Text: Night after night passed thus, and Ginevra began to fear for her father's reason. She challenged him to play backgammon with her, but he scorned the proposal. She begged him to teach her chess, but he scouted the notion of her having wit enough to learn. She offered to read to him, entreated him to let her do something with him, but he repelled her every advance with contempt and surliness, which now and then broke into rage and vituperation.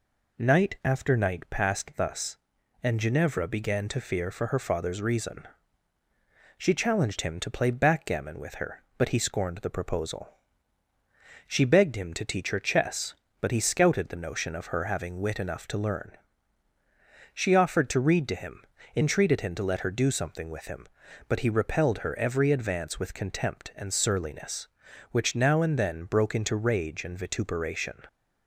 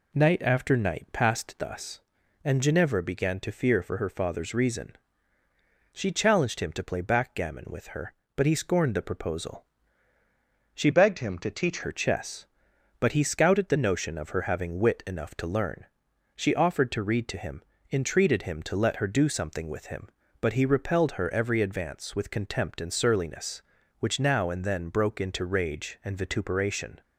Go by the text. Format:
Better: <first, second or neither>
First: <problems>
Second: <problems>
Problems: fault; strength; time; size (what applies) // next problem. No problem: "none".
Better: first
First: none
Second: changes voice from "begged" to "teach"; from 10.9 to 11.8 s; 0.9 s long